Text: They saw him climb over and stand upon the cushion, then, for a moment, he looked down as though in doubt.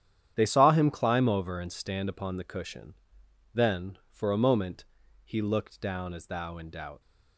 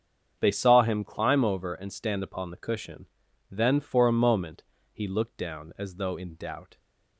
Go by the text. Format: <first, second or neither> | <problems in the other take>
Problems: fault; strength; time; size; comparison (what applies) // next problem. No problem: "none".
second | starts louder than the rest; strong; until 1.3 s; 9.5 dB; strong in the second // says "thou" for "though"; at 6.2 s